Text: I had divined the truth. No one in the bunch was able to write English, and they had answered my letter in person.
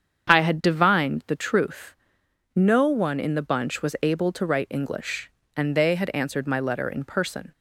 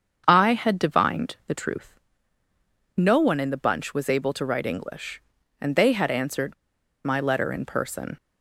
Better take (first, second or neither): first